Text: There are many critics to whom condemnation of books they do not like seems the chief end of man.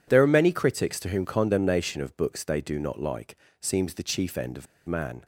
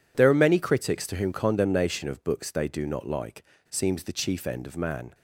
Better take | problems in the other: second | pauses between "like" and "seems"; slight; at 3.3 s; 0.26 s long; slight in the second // pauses between "of" and "man"; slight; at 4.6 s; 0.20 s long

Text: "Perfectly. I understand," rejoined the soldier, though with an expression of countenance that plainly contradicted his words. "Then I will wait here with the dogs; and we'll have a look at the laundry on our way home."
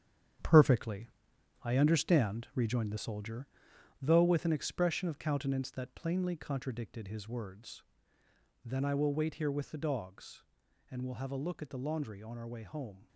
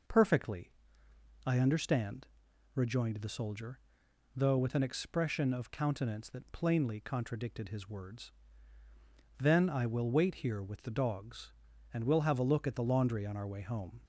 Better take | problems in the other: second | gets quieter; strong; throughout; 8.5 dB

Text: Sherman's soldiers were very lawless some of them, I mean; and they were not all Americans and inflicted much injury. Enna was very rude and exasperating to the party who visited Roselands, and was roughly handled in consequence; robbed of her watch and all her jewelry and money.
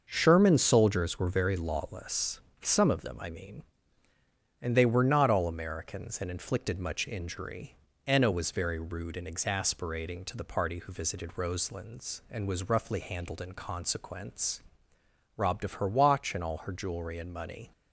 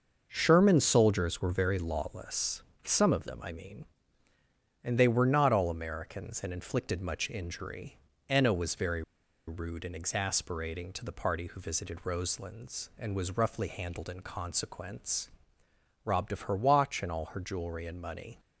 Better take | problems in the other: first | starts louder than the rest; noticeable; until 1.3 s; 6 dB; noticeable in the first // pauses between "lawless" and "some"; slight; at 2.6 s; 0.22 s long; slight in the first // pauses between "very" and "rude"; at 9.0 s; 0.45 s long

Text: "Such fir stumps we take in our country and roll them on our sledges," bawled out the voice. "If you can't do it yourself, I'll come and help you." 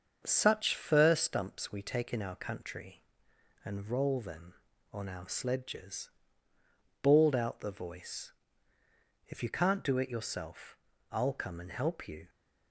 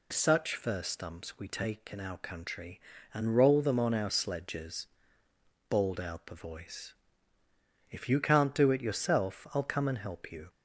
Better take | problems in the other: second | gets quieter; slight; throughout; 2.5 dB

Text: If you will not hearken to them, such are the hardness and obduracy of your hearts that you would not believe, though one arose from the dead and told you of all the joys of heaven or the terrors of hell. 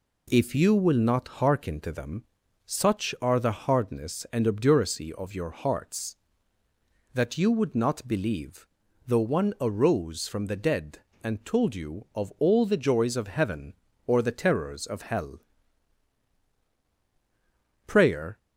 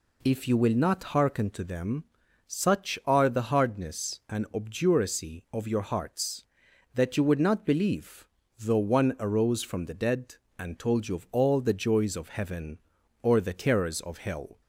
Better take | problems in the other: second | goes on to say "Prayer"; from 17.8 s on; 0.52 s long

